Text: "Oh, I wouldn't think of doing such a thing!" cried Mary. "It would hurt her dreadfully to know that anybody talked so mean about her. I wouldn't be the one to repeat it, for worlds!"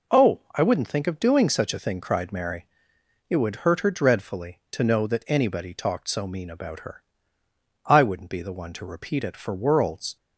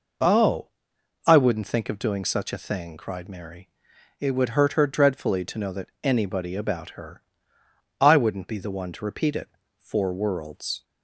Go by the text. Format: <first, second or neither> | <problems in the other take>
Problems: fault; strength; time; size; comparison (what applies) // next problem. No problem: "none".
first | skips "talked so mean"; at 6.5 s